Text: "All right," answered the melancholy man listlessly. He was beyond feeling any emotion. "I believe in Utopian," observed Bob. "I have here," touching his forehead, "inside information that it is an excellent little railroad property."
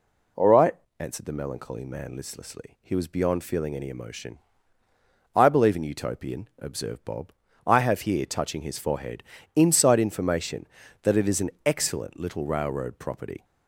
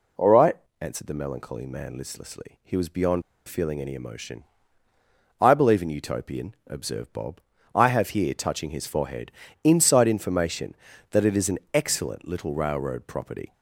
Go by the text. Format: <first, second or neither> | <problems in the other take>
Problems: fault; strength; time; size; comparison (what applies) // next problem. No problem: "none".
first | pauses between "beyond" and "feeling"; slight; at 3.2 s; 0.28 s long // pauses between "an" and "excellent"; slight; at 11.5 s; 0.16 s long; slight in the first